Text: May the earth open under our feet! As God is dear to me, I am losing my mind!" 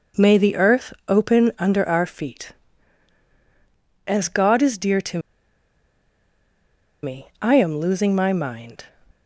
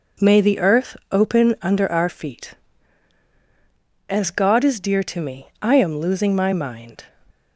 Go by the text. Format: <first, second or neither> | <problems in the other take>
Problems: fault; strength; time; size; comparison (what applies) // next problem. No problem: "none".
second | pauses between "earth" and "open"; slight; at 0.9 s; 0.16 s long; slight in the second // pauses between "to" and "me"; strong; at 5.1 s; 1.8 s long